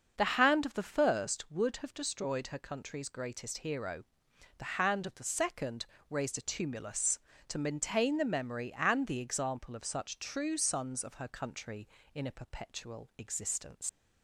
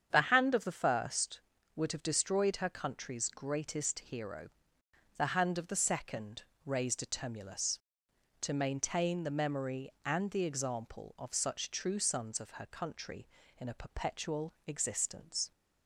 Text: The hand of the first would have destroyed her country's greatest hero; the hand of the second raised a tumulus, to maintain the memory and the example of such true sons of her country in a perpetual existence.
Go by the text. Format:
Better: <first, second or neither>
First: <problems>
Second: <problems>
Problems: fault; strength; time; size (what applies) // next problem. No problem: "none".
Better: second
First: starts louder than the rest; until 1.1 s; 6.5 dB // pauses between "second" and "raised"; slight; at 5.8 s; 0.24 s long // leaves "existence" unfinished; at 13.8 s; 65 ms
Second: starts louder than the rest; strong; until 1.1 s; 8 dB // pauses between "second" and "raised"; slight; at 6.4 s; 0.22 s long